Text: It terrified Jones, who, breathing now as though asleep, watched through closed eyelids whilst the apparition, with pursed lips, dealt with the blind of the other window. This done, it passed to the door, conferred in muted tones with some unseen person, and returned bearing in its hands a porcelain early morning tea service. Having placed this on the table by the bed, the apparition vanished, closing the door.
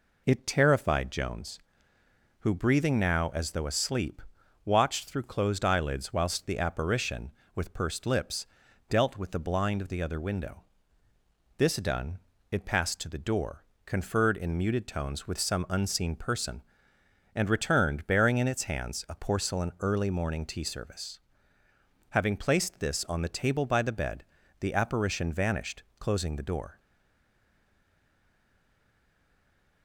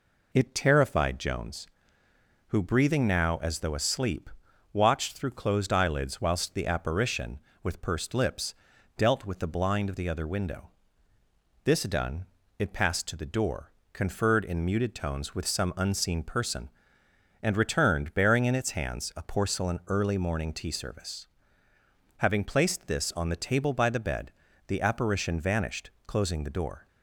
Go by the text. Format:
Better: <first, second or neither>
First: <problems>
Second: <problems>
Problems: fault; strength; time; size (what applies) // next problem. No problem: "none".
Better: second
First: stays silent after the last word; strong; from 26.7 s on; 3.1 s long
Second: none